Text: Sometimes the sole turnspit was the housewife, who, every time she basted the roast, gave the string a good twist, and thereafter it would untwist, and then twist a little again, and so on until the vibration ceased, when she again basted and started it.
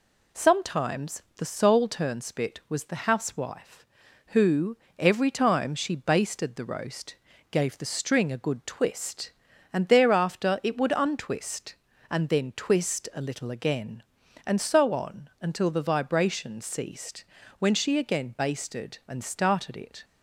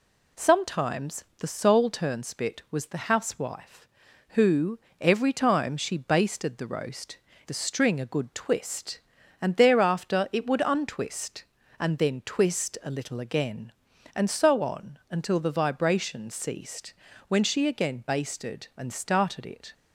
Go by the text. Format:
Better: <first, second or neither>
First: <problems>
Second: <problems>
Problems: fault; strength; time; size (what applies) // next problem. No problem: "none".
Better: first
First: pauses between "Sometimes" and "the"; slight; at 1.2 s; 0.16 s long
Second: pauses between "Sometimes" and "the"; slight; at 1.2 s; 0.16 s long // skips "gave"; at 7.3 s